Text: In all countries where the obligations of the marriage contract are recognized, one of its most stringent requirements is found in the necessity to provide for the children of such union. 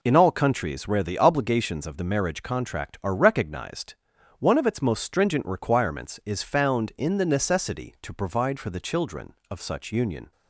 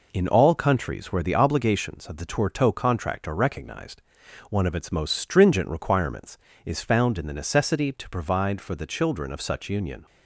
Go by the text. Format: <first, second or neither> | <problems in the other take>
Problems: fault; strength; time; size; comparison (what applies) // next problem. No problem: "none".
first | says "tourteau" for "marriage"; at 2.2 s